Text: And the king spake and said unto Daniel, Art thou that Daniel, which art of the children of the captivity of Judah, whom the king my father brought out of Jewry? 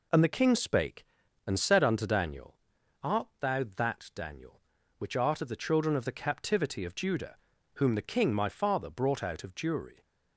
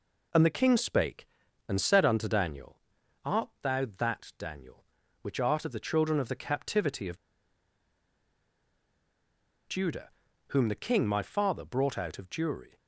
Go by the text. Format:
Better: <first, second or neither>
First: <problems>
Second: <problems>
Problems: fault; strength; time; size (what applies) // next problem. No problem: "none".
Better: first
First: none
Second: pauses between "of" and "Judah"; strong; at 7.1 s; 2.5 s long